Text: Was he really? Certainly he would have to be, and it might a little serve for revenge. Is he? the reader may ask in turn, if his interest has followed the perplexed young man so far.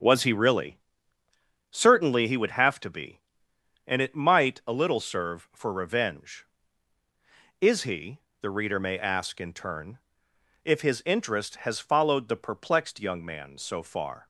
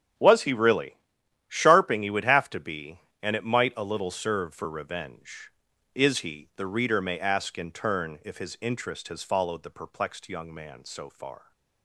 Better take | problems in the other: first | starts louder than the rest; strong; until 1.6 s; 8.5 dB; strong in the first // says "Sharping" for "Certainly"; at 1.4 s

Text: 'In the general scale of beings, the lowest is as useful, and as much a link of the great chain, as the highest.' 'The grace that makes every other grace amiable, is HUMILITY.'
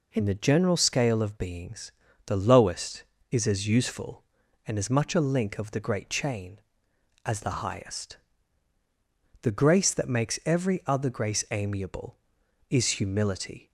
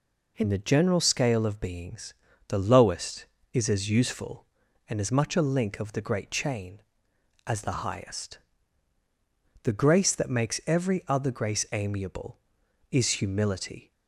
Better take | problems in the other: neither | none

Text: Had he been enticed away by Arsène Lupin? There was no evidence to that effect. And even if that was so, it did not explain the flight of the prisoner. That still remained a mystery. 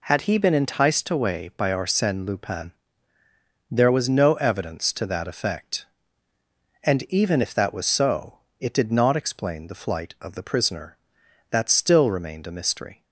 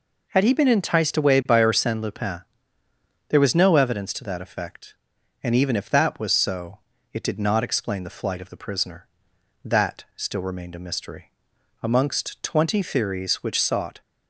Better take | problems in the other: first | goes on to say "Amongst twenty theories which sought"; strong; from 11.8 s on; 2.1 s long

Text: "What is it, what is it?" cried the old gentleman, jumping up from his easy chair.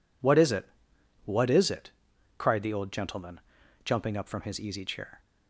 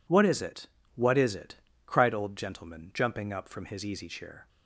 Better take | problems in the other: first | skips "the"; at 2.1 s

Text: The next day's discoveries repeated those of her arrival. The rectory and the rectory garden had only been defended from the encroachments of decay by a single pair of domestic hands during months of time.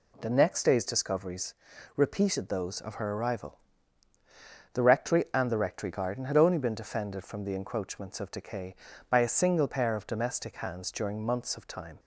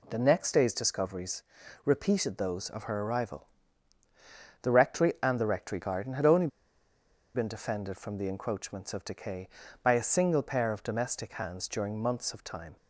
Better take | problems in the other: first | pauses between "discoveries" and "repeated"; at 1.4 s; 0.42 s long; also in the first // pauses between "only" and "been"; noticeable; at 6.4 s; 0.87 s long

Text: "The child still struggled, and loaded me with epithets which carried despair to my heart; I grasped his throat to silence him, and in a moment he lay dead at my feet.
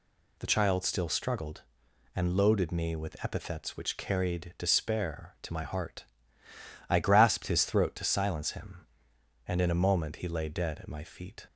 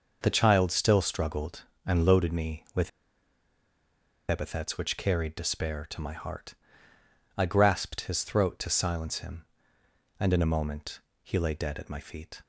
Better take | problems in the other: first | pauses between "with" and "epithets"; strong; at 2.8 s; 1.4 s long // pauses between "moment" and "he"; slight; at 11.0 s; 0.22 s long

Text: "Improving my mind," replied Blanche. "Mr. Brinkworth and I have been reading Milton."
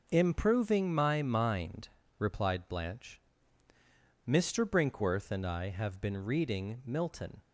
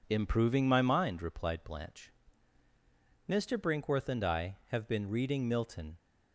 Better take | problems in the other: neither | none

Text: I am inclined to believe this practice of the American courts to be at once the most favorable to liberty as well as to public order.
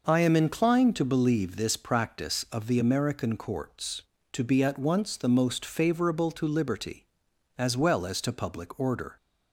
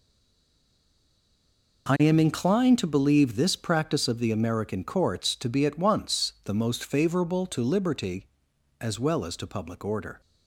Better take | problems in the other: first | stays silent before the first word; noticeable; until 1.8 s; 1.8 s long

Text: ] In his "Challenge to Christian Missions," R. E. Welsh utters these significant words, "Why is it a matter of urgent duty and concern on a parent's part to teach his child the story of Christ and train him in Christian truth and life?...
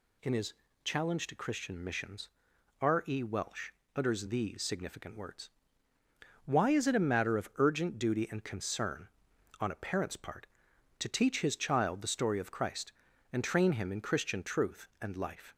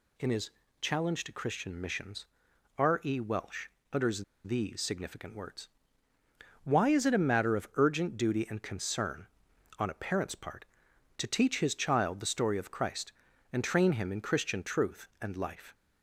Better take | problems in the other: first | pauses between "his" and "Challenge"; slight; at 0.5 s; 0.30 s long; slight in the first // pauses between "Welsh" and "utters"; slight; at 3.6 s; 0.26 s long; slight in the first // pauses between "utters" and "these"; slight; at 4.2 s; 0.20 s long

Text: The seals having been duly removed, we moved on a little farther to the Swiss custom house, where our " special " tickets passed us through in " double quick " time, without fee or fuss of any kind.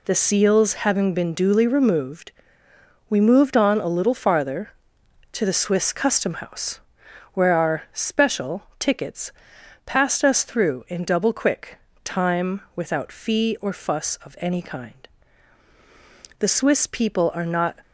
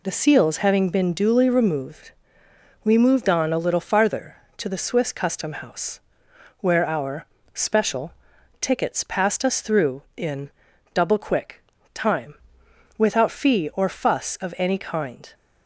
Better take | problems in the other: second | pauses between "tickets" and "passed"; noticeable; at 9.3 s; 0.54 s long // goes on to say "The Swiss people are not"; from 16.3 s on; 1.3 s long

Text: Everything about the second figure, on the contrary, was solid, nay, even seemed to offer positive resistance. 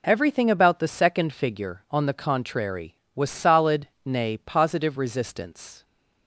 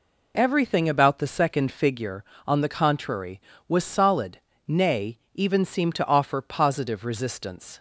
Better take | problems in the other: second | skips "even seemed to offer"; at 4.3 s

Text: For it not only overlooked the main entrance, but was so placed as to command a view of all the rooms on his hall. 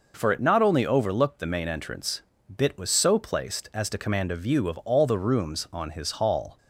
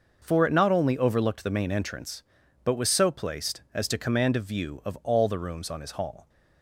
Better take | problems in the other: second | says "bit" for "but"; at 2.5 s

